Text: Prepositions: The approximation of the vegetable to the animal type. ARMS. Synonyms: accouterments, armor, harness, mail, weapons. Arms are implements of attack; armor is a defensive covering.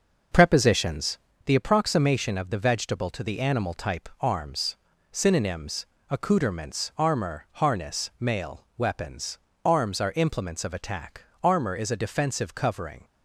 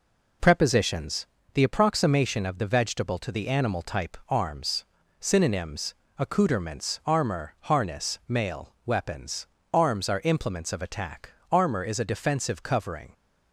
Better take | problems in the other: second | starts louder than the rest; noticeable; until 1.5 s; 6 dB

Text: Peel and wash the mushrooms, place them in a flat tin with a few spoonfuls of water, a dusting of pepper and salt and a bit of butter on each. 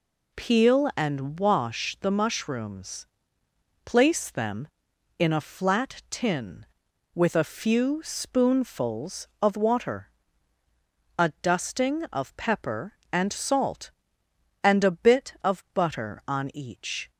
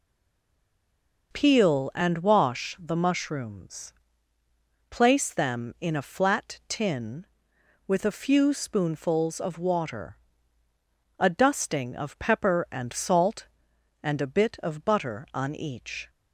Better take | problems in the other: first | stays silent before the first word; noticeable; until 1.3 s; 1.3 s long

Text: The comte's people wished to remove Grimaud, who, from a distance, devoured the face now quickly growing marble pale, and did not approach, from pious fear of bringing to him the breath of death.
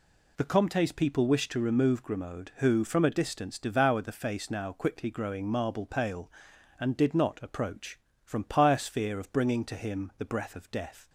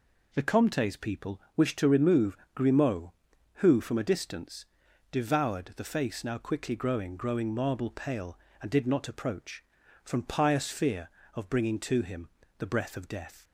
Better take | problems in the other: first | pauses between "people" and "wished"; slight; at 1.4 s; 0.16 s long // pauses between "remove" and "Grimaud"; slight; at 2.3 s; 0.16 s long // says "growing" twice; at 7.1 s // pauses between "him" and "the"; slight; at 12.2 s; 0.30 s long

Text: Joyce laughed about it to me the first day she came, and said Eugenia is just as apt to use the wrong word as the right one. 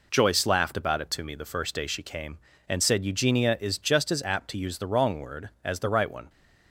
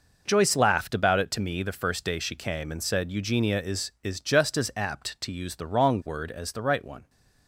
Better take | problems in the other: first | says "is" twice; at 4.0 s

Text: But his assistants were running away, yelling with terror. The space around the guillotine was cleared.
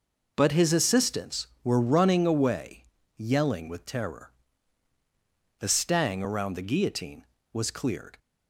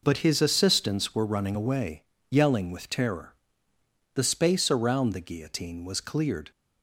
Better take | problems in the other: second | says "stang" for "space"; at 5.6 s

